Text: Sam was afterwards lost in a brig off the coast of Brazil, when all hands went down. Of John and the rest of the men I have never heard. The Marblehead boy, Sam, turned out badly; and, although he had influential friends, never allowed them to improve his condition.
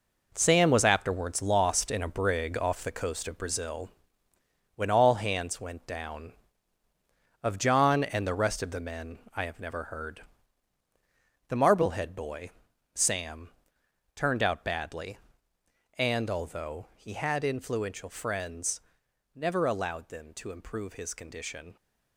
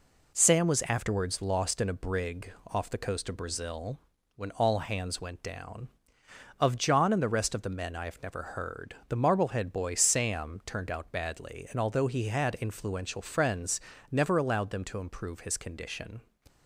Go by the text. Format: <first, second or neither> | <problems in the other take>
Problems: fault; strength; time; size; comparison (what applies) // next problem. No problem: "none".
second | gets quieter; strong; throughout; 9 dB // pauses between "men" and "I"; slight; at 9.1 s; 0.18 s long